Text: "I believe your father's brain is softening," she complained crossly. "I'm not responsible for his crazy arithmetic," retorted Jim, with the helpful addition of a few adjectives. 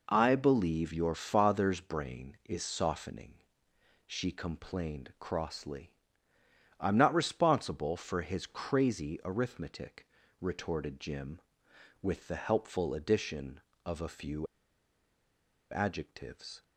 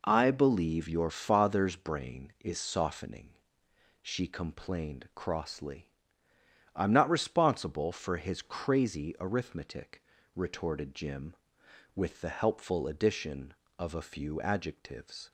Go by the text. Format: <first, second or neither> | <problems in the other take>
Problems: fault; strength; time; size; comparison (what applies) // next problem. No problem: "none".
second | pauses between "few" and "adjectives"; strong; at 14.4 s; 1.2 s long